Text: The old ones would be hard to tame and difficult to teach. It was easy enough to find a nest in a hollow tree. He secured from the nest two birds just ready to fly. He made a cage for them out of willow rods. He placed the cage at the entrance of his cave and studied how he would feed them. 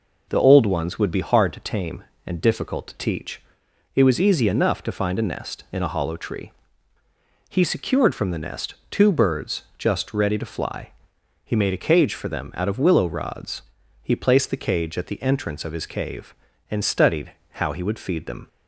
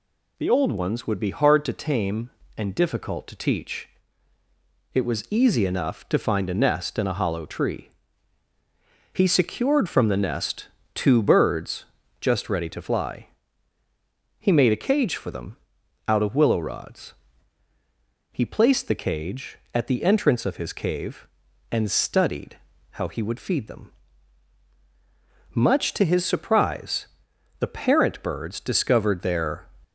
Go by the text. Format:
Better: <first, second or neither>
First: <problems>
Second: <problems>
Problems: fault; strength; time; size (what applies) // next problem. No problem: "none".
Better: first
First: pauses between "nest" and "two"; slight; at 8.7 s; 0.16 s long // pauses between "birds" and "just"; slight; at 9.6 s; 0.16 s long // pauses between "studied" and "how"; slight; at 17.3 s; 0.20 s long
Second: pauses between "nest" and "two"; slight; at 10.6 s; 0.26 s long // pauses between "birds" and "just"; slight; at 11.8 s; 0.34 s long // pauses between "them" and "out"; noticeable; at 15.5 s; 0.52 s long // pauses between "studied" and "how"; slight; at 22.5 s; 0.34 s long // goes on to say "Much to his surprise the parent birds discovered their"; strong; from 25.5 s on; 4.1 s long